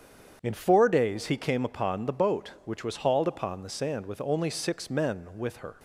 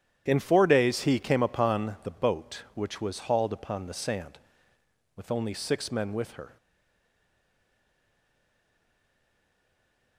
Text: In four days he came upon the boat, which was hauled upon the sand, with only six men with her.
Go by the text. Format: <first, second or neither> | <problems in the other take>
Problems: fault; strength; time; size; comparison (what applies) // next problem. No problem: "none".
first | starts louder than the rest; strong; until 1.2 s; 10 dB; strong in the first // stays silent after the last word; strong; from 6.5 s on; 3.6 s long